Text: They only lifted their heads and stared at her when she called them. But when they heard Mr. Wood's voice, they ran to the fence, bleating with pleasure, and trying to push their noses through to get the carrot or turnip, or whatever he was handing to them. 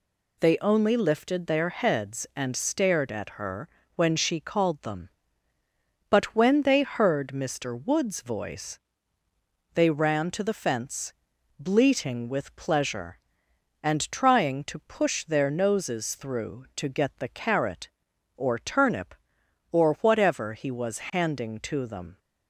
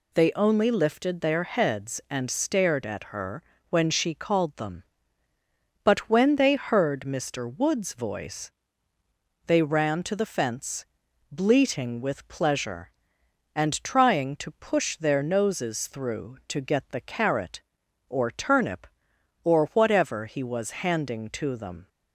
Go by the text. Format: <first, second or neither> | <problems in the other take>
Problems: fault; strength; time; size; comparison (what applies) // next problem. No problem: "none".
neither | pauses between "her" and "when"; slight; the same in both